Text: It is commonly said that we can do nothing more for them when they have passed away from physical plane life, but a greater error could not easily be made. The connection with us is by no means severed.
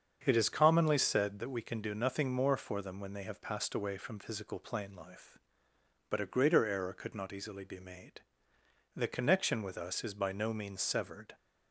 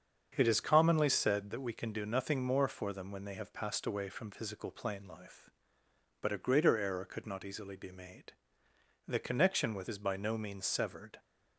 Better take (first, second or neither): first